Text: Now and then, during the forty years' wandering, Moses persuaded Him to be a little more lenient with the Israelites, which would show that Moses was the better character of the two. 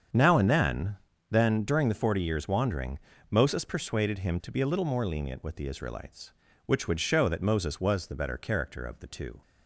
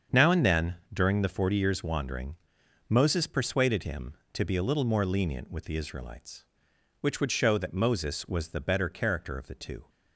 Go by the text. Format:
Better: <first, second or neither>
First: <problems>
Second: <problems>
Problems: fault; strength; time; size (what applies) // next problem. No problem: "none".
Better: second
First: starts louder than the rest; strong; until 1.4 s; 7.5 dB // says "then" twice; at 1.3 s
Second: starts louder than the rest; strong; until 1.3 s; 7 dB